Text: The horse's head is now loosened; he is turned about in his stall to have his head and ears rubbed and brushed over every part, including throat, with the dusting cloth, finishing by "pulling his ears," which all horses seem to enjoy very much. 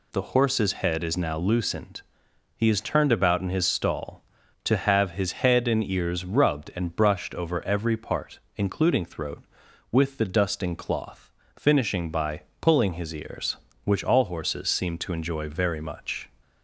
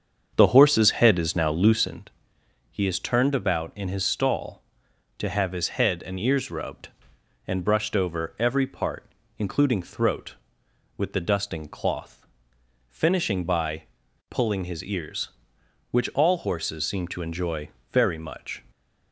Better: first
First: pauses between "by" and "pulling"; slight; at 12.4 s; 0.22 s long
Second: starts louder than the rest; strong; until 2.0 s; 7 dB // pauses between "by" and "pulling"; at 13.8 s; 0.45 s long // pauses between "enjoy" and "very"; slight; at 17.6 s; 0.22 s long

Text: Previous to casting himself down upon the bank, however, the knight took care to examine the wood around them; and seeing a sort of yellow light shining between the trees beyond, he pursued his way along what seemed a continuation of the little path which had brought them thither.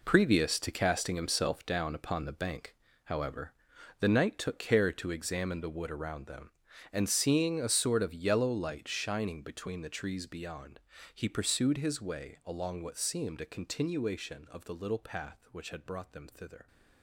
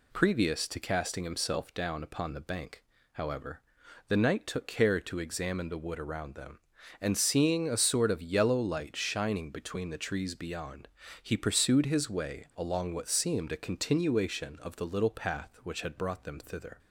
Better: second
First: gets quieter; strong; throughout; 11.5 dB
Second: none

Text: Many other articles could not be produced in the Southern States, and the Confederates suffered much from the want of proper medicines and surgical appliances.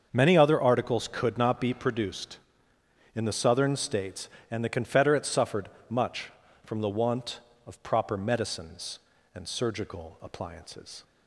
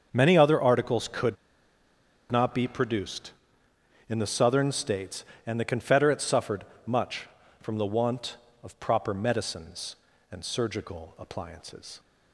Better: first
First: starts louder than the rest; until 1.1 s; 7 dB // pauses between "suffered" and "much"; slight; at 5.6 s; 0.20 s long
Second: starts louder than the rest; until 1.1 s; 7 dB // pauses between "could" and "not"; noticeable; at 1.3 s; 0.95 s long // pauses between "suffered" and "much"; slight; at 6.6 s; 0.22 s long

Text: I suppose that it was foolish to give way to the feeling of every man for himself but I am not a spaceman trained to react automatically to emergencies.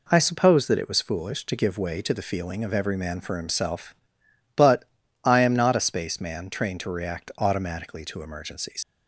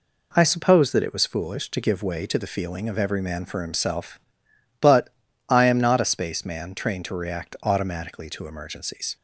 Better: second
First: pauses between "but" and "I"; at 4.8 s; 0.38 s long // leaves "emergencies" unfinished; at 8.8 s; 85 ms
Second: pauses between "but" and "I"; at 5.0 s; 0.38 s long

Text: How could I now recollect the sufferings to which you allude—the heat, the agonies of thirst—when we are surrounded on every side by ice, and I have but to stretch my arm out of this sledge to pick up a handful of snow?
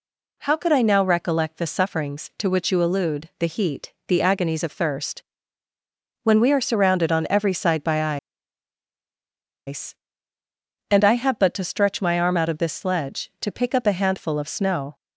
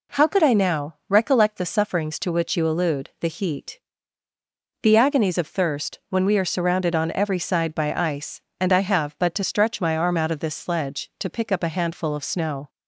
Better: second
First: pauses between "by" and "ice"; strong; at 8.1 s; 1.4 s long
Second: none

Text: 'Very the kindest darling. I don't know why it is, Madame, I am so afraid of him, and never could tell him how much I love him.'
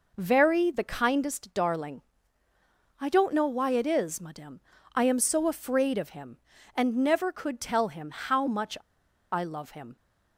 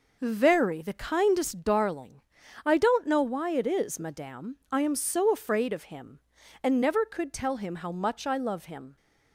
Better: second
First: pauses between "much" and "I"; noticeable; at 8.7 s; 0.53 s long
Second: none

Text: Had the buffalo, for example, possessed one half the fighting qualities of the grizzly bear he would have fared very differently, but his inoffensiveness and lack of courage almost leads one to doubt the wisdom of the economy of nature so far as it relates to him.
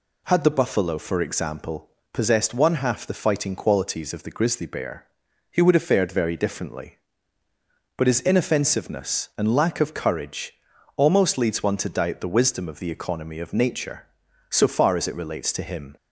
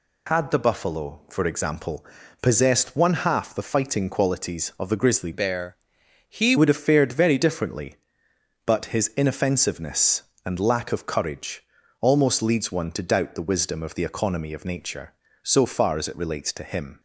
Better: first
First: pauses between "bear" and "he"; at 5.0 s; 0.44 s long // pauses between "courage" and "almost"; at 10.5 s; 0.43 s long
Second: changes voice from "bear" to "he"; from 5.3 to 6.5 s; 1.2 s long // pauses between "bear" and "he"; noticeable; at 5.7 s; 0.52 s long // pauses between "courage" and "almost"; at 11.6 s; 0.38 s long

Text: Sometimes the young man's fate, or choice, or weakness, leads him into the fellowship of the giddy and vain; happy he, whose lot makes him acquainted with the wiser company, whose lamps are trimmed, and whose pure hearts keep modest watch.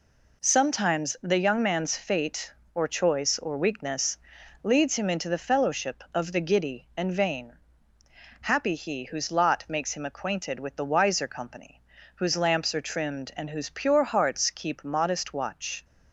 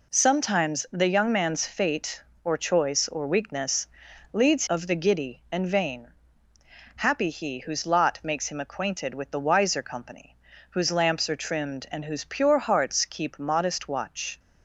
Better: first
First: none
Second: skips "him into the fellowship"; at 4.6 s

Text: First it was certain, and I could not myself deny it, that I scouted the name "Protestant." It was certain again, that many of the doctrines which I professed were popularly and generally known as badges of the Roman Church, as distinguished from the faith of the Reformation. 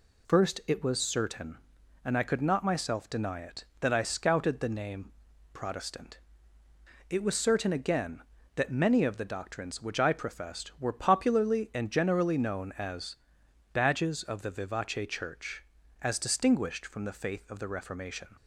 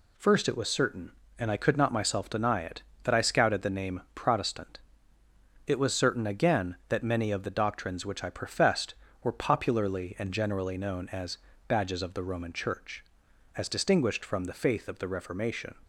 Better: second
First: pauses between "name" and "Protestant"; at 5.1 s; 0.42 s long // pauses between "as" and "badges"; noticeable; at 13.1 s; 0.56 s long // says "Vivace" for "Roman"; at 14.4 s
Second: pauses between "as" and "badges"; slight; at 11.3 s; 0.30 s long

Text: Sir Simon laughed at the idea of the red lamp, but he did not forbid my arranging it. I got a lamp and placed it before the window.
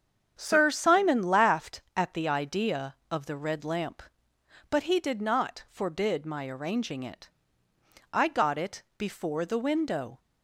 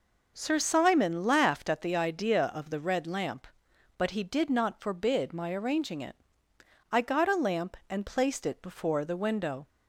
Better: second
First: starts louder than the rest; strong; until 1.3 s; 8 dB // skips "a lamp and placed"; at 8.5 s // pauses between "it" and "before"; slight; at 8.8 s; 0.16 s long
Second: none

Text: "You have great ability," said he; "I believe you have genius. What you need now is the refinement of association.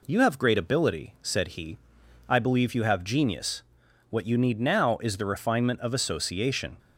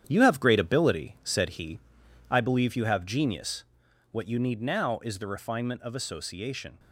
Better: first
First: none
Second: gets quieter; strong; throughout; 7 dB

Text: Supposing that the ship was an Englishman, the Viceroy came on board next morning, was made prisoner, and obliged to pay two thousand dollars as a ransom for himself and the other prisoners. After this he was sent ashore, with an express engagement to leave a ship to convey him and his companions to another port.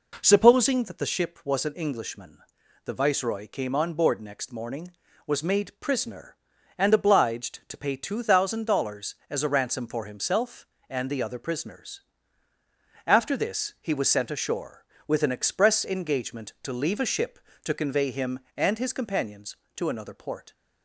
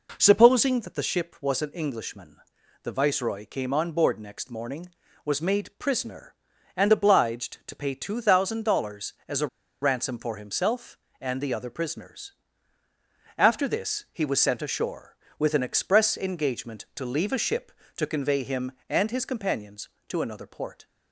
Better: first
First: none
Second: pauses between "a" and "ransom"; slight; at 9.4 s; 0.35 s long

